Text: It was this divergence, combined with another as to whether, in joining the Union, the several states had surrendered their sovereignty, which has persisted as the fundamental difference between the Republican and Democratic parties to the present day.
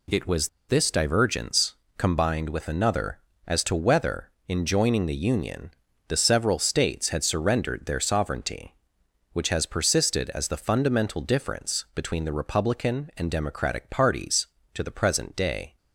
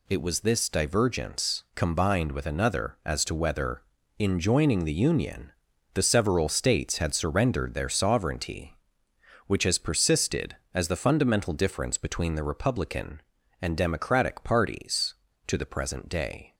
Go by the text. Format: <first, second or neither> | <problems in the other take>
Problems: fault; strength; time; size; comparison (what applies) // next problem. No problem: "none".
second | pauses between "was" and "this"; slight; at 0.4 s; 0.21 s long